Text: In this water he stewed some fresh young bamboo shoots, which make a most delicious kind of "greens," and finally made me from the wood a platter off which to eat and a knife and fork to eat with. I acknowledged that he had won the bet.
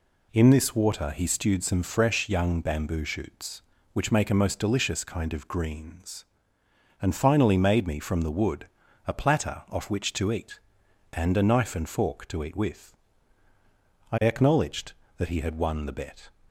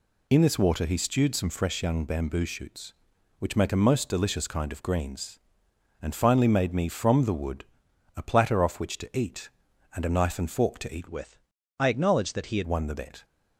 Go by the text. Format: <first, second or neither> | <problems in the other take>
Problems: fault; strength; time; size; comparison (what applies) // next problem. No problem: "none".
first | pauses between "wood" and "a"; noticeable; at 7.6 s; 0.52 s long; also in the first // changes voice from "with" to "had"; from 11.0 to 12.6 s; 1.6 s long